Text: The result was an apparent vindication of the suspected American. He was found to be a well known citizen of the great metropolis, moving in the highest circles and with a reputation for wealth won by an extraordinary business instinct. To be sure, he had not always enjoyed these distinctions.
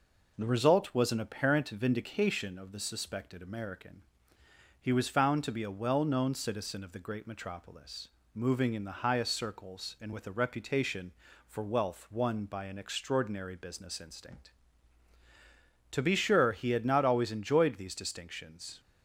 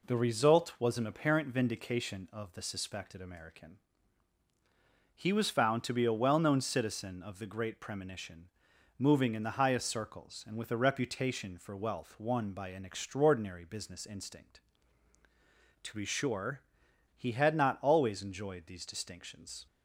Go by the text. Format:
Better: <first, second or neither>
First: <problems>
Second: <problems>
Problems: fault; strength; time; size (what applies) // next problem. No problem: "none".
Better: first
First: none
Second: says "premonition" for "metropolis"; at 7.8 s